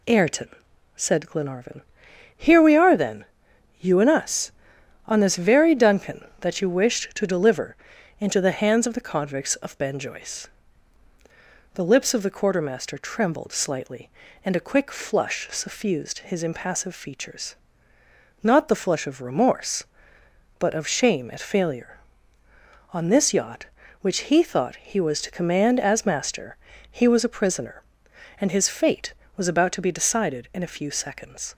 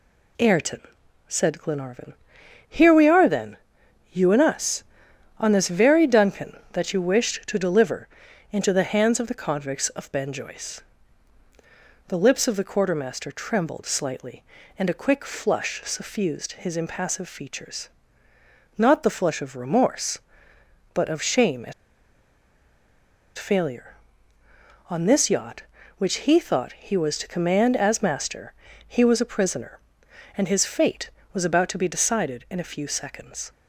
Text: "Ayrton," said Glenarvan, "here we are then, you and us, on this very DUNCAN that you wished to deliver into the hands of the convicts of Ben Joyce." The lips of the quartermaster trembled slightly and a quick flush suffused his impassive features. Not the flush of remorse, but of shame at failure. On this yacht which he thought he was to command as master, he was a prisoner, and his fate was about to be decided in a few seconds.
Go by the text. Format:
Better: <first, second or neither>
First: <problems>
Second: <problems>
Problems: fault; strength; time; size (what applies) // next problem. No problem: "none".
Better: first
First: pauses between "deliver" and "into"; at 7.7 s; 0.42 s long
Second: pauses between "deliver" and "into"; at 8.0 s; 0.42 s long // pauses between "at" and "failure"; strong; at 21.7 s; 1.6 s long